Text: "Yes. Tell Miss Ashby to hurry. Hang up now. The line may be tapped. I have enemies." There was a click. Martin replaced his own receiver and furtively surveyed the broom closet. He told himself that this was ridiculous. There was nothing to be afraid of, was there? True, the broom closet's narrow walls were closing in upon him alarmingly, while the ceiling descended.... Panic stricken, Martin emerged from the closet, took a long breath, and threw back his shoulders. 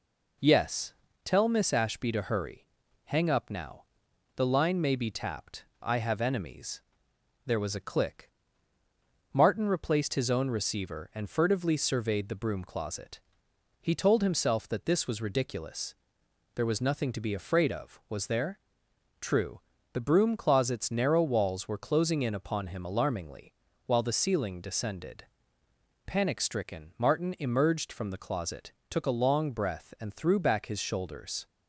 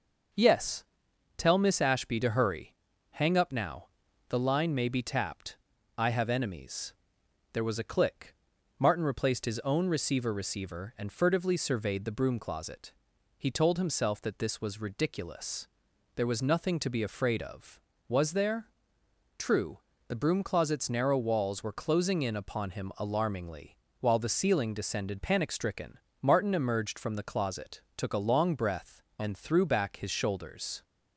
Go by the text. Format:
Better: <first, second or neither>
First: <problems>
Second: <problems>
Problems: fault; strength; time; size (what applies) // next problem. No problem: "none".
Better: first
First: none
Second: starts louder than the rest; noticeable; until 1.8 s; 6 dB // says "receiver" twice; at 10.3 s